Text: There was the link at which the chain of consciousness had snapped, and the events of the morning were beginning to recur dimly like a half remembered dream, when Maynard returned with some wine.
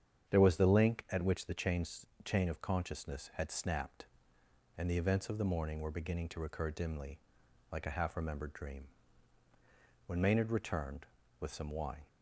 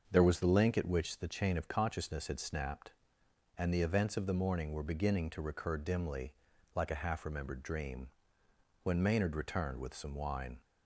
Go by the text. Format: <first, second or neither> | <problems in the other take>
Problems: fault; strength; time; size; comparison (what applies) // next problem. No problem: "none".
second | starts louder than the rest; strong; until 1.3 s; 8.5 dB; also in the second // says "chain" twice; at 2.2 s // pauses between "dimly" and "like"; noticeable; at 7.1 s; 0.52 s long; also in the second